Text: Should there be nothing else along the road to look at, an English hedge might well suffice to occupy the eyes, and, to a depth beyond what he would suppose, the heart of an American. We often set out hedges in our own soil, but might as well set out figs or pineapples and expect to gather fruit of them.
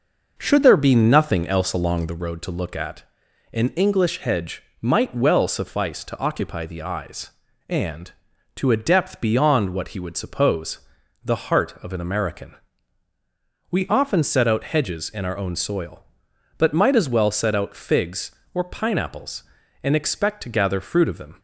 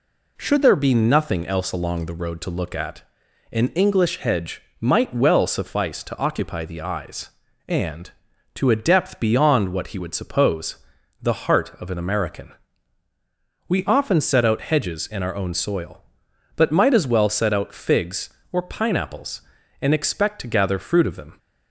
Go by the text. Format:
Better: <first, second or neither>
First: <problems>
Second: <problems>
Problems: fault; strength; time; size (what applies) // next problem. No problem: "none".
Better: second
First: starts louder than the rest; noticeable; until 2.3 s; 5.5 dB // pauses between "hedge" and "might"; slight; at 4.6 s; 0.18 s long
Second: pauses between "hedge" and "might"; slight; at 4.6 s; 0.18 s long